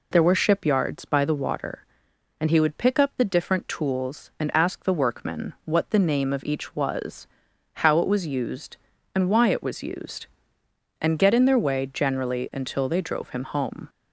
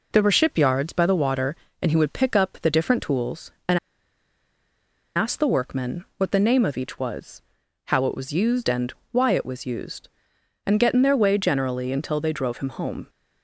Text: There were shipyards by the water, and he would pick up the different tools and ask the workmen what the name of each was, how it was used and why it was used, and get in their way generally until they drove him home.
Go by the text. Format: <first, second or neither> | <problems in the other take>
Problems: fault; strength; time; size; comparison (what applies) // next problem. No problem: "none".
first | pauses between "and" and "ask"; strong; at 3.7 s; 1.3 s long // pauses between "and" and "why"; slight; at 8.9 s; 0.18 s long